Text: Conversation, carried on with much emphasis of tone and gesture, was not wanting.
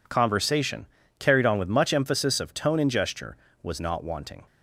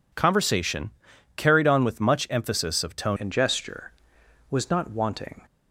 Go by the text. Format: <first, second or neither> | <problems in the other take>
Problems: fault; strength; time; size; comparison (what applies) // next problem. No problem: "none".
first | changes voice at "and"; from 3.1 s on; 2.3 s long